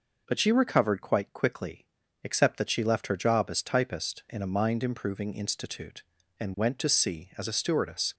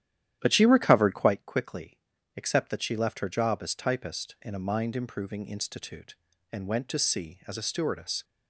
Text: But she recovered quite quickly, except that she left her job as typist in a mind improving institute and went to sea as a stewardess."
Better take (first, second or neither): first